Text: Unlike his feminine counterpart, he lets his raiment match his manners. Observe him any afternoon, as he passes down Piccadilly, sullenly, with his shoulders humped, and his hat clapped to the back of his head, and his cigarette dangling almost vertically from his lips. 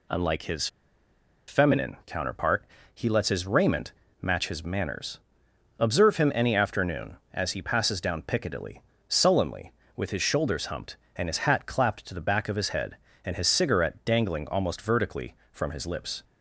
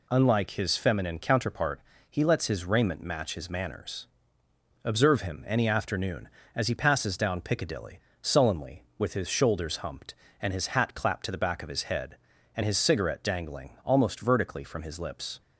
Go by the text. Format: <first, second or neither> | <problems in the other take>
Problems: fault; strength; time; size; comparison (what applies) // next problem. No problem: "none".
second | pauses between "his" and "feminine"; noticeable; at 0.6 s; 0.80 s long // pauses between "raiment" and "match"; slight; at 3.9 s; 0.30 s long